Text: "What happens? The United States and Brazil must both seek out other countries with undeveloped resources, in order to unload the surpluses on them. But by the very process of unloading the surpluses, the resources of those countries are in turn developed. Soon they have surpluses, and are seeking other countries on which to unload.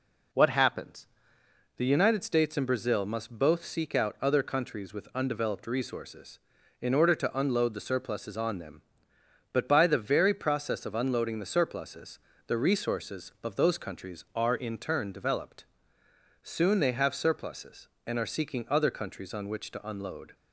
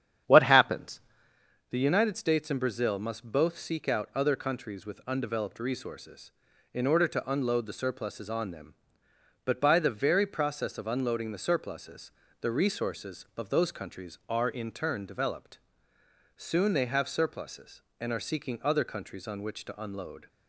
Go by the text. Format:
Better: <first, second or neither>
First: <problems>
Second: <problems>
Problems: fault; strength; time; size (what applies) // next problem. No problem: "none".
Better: first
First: none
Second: starts louder than the rest; strong; until 1.3 s; 9 dB